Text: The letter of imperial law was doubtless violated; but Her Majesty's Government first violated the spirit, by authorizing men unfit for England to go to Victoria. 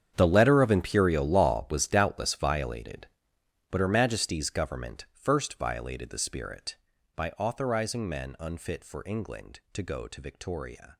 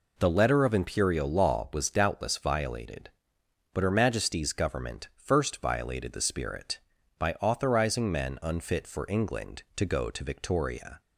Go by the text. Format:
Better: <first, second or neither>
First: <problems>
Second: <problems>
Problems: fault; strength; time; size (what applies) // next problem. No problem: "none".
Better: second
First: gets quieter; strong; throughout; 17 dB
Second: none